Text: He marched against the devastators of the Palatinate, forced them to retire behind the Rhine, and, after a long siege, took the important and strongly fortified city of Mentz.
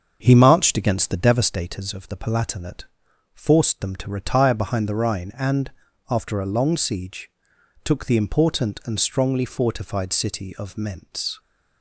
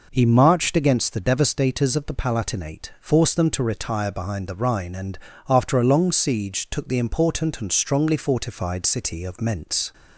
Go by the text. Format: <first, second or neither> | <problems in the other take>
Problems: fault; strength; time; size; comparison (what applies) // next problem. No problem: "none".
second | starts louder than the rest; until 1.6 s; 6.5 dB